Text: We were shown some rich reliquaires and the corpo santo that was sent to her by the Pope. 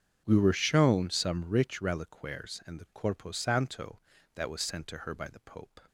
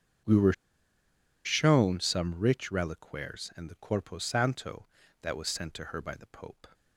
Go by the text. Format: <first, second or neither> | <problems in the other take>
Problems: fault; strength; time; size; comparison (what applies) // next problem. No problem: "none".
first | starts louder than the rest; strong; until 2.1 s; 7.5 dB; strong in the first // pauses between "were" and "shown"; noticeable; at 0.5 s; 0.91 s long